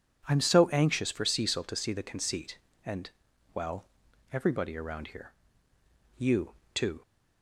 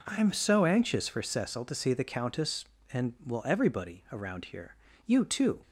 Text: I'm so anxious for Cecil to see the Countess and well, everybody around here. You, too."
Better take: second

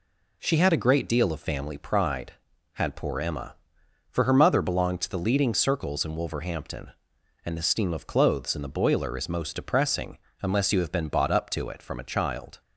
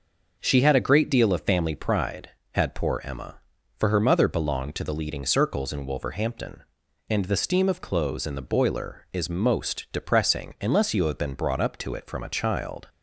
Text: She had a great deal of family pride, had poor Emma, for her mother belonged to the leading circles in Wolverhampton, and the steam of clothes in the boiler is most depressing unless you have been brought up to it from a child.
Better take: second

